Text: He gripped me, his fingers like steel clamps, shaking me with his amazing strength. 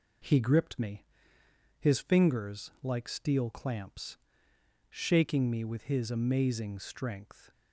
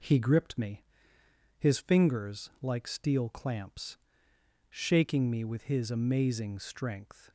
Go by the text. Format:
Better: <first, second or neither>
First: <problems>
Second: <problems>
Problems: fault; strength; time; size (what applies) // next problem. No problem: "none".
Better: neither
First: none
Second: none